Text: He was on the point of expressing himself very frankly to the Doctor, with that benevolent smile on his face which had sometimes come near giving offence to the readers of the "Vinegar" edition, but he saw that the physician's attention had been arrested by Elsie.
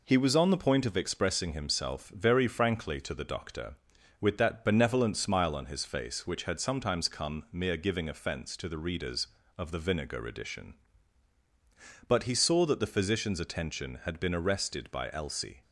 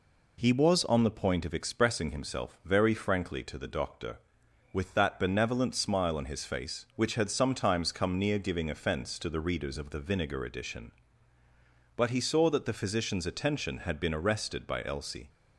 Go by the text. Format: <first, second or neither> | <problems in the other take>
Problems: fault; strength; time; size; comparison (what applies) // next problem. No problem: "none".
second | says "mere" for "near"; at 7.5 s